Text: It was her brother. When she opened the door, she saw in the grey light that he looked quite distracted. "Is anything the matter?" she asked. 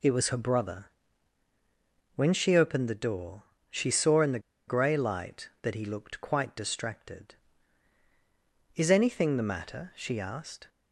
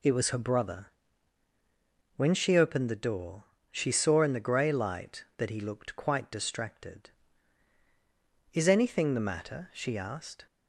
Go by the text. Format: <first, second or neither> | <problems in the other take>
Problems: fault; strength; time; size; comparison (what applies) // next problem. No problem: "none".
second | pauses between "the" and "grey"; slight; at 4.3 s; 0.28 s long